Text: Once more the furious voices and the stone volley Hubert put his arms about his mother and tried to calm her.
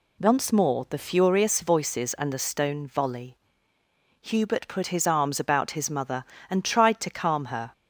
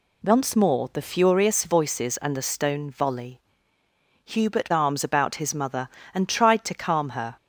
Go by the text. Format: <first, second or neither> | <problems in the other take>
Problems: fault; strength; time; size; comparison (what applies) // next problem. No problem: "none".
first | pauses between "volley" and "Hubert"; noticeable; at 3.3 s; 0.86 s long; noticeable in the first // skips "put his"; at 4.6 s